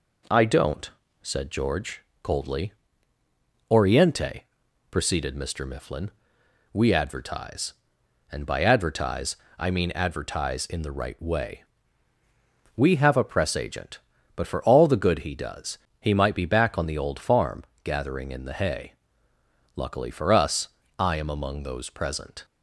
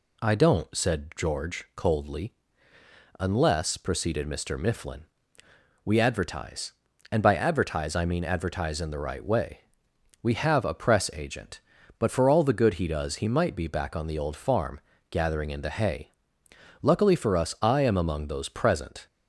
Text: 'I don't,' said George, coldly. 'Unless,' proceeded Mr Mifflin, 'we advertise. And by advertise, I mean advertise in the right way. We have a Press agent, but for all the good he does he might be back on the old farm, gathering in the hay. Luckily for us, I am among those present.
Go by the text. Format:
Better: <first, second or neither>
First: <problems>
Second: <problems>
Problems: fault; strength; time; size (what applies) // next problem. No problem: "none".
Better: second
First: says "Oriente" for "Unless"; at 3.7 s // pauses between "does" and "he"; slight; at 15.7 s; 0.22 s long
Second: none